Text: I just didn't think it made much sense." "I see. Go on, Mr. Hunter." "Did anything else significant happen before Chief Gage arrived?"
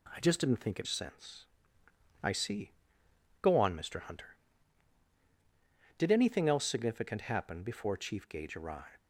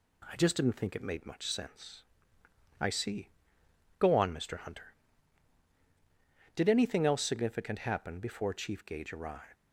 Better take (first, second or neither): second